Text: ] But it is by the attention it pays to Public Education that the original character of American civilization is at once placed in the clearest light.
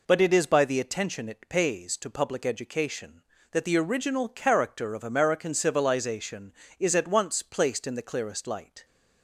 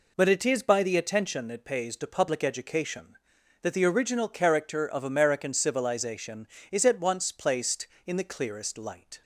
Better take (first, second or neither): neither